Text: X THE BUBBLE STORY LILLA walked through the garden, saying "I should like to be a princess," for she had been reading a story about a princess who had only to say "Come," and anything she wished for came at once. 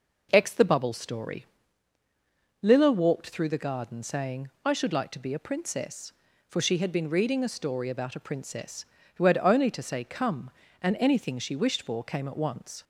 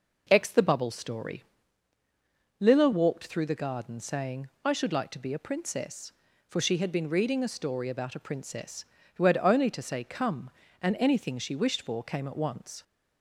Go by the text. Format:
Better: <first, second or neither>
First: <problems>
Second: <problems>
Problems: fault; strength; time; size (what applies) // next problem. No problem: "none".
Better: neither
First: pauses between "STORY" and "LILLA"; at 1.4 s; 1.1 s long // pauses between "saying" and "I"; slight; at 4.5 s; 0.15 s long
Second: pauses between "STORY" and "LILLA"; at 1.4 s; 1.1 s long // pauses between "saying" and "I"; slight; at 4.4 s; 0.16 s long